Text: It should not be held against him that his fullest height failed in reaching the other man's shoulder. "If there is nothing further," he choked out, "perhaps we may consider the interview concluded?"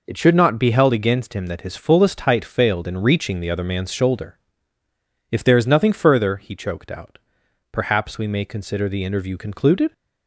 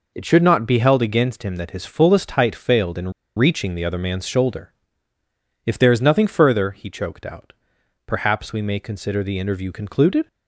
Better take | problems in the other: first | pauses between "in" and "reaching"; slight; at 3.1 s; 0.24 s long

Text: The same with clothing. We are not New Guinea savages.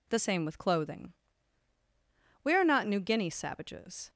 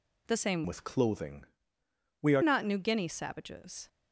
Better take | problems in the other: first | changes voice from "with" to "are"; from 0.6 to 2.4 s; 1.8 s long

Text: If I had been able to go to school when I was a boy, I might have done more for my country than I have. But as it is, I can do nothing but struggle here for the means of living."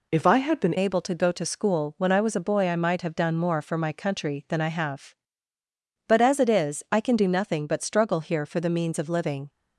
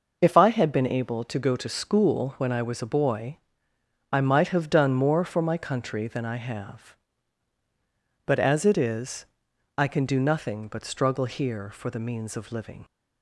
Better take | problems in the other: second | changes voice at "able"; from 0.7 s on; 8.7 s long

